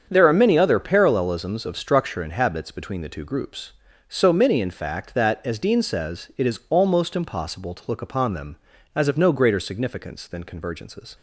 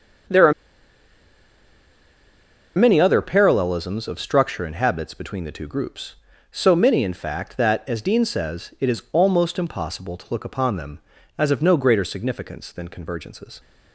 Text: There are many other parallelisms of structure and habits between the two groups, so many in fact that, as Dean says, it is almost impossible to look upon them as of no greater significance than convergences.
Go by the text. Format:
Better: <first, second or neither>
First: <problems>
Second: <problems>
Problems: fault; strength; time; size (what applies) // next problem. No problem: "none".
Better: first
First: starts louder than the rest; strong; until 1.1 s; 7.5 dB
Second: starts louder than the rest; strong; until 3.5 s; 7.5 dB // pauses between "are" and "many"; strong; at 0.5 s; 2.2 s long